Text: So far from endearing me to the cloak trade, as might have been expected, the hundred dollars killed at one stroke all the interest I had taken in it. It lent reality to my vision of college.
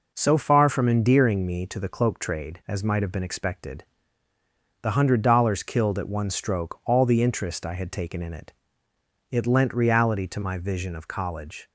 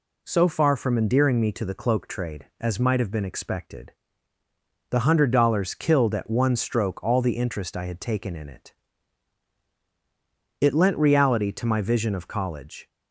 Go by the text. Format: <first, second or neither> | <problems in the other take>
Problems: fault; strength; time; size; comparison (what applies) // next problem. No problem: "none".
neither | none